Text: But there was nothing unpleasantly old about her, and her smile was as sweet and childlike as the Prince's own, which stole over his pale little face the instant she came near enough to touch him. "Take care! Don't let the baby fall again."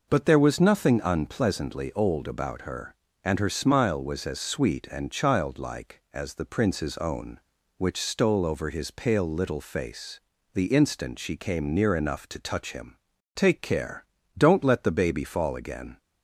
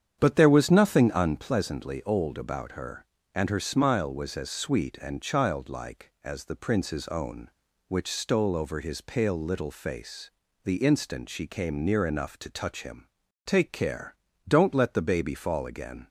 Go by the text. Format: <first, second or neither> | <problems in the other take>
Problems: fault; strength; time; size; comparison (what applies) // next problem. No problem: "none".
first | starts louder than the rest; strong; until 1.5 s; 8.5 dB // pauses between "face" and "the"; slight; at 10.3 s; 0.34 s long; slight in the first